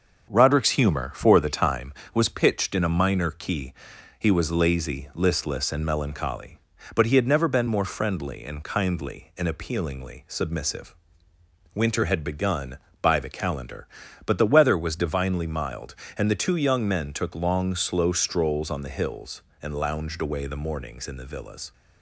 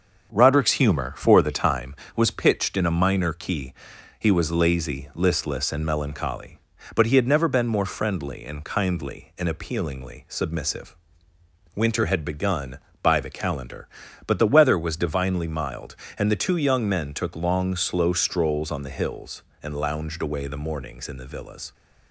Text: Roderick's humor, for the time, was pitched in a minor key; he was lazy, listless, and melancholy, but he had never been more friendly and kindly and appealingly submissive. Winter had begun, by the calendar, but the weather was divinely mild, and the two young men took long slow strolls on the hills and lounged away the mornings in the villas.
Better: neither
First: starts louder than the rest; until 1.3 s; 7 dB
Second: starts louder than the rest; until 1.3 s; 7 dB

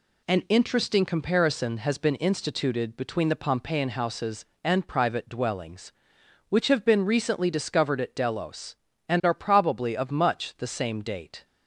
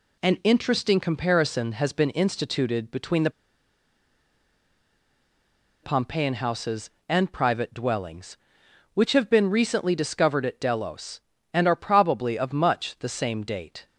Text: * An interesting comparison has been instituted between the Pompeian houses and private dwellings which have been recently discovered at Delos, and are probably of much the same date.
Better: first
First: none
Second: pauses between "the" and "Pompeian"; strong; at 3.2 s; 2.5 s long

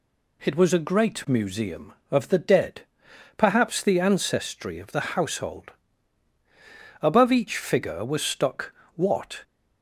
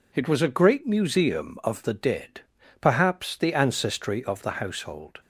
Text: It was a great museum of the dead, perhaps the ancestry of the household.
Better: second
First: goes on to say "Above each figure was stuck what"; strong; from 7.0 s on; 2.4 s long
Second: none

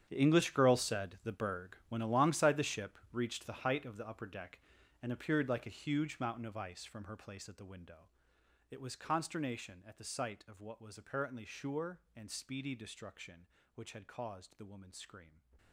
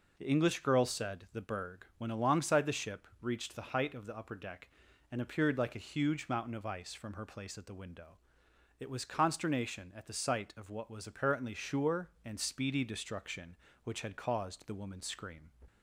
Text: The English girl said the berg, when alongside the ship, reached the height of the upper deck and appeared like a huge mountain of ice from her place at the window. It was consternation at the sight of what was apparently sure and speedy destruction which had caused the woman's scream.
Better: second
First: gets quieter; strong; throughout; 16.5 dB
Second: none

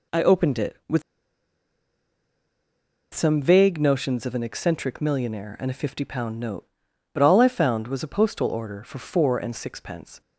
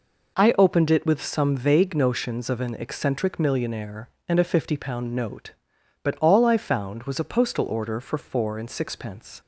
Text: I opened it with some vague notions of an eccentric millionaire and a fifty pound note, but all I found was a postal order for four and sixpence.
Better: second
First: pauses between "with" and "some"; strong; at 1.0 s; 2.1 s long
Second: none

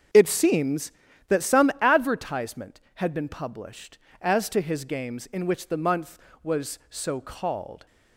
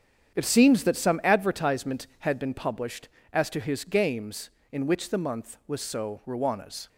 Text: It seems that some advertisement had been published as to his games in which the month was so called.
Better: first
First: starts louder than the rest; until 1.5 s; 7 dB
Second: starts louder than the rest; strong; until 1.3 s; 8.5 dB // says "ruanas" for "called"; at 6.2 s

